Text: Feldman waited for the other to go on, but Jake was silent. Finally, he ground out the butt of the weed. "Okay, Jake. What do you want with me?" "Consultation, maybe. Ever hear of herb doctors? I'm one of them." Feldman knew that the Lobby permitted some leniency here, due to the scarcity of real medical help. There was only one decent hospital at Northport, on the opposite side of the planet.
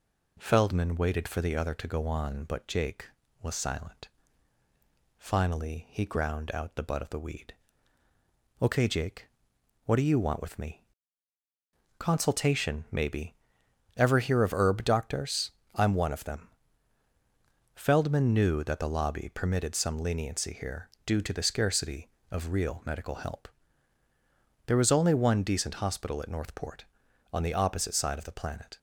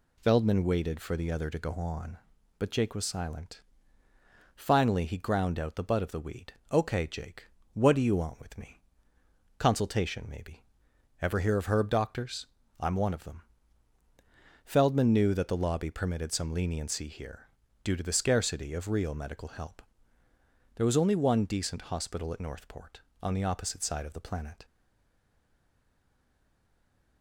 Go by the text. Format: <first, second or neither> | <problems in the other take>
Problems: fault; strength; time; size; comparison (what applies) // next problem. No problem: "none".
first | stays silent after the last word; strong; from 24.6 s on; 2.6 s long